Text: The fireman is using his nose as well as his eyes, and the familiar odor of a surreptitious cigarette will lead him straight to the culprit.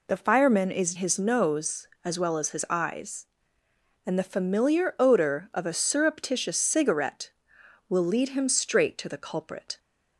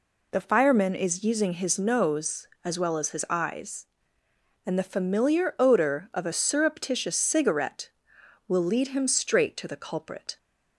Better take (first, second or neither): second